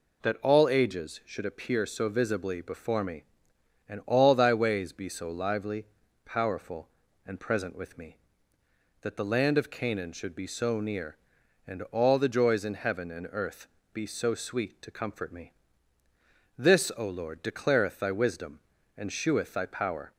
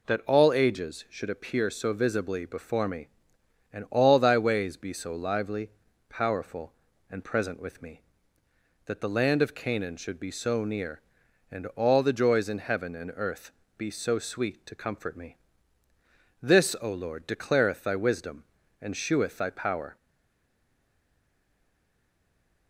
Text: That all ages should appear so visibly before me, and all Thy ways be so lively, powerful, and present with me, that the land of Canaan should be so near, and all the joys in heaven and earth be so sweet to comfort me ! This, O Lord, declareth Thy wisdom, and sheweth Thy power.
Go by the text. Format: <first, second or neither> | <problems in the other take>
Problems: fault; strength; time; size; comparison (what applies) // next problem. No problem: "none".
first | pauses between "earth" and "be"; slight; at 13.5 s; 0.26 s long; slight in the first // stays silent after the last word; strong; from 19.9 s on; 2.7 s long